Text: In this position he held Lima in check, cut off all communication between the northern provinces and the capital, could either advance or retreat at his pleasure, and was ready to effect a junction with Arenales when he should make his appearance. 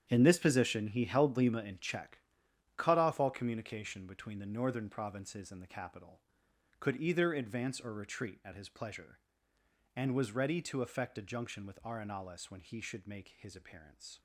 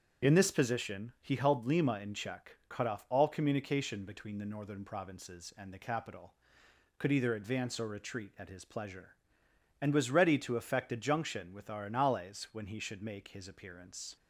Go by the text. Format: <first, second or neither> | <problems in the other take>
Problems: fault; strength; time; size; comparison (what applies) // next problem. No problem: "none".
second | gets quieter; strong; throughout; 13 dB // starts louder than the rest; strong; until 1.1 s; 9 dB; strong in the second